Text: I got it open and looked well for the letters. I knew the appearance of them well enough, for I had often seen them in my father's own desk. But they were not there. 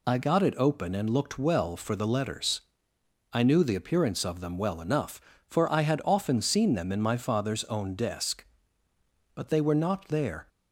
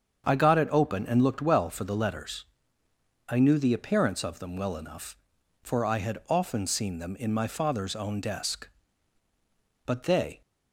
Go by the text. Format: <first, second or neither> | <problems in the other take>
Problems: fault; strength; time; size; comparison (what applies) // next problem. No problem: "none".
first | starts louder than the rest; strong; until 1.2 s; 7 dB // stops before "were not there"; at 10.4 s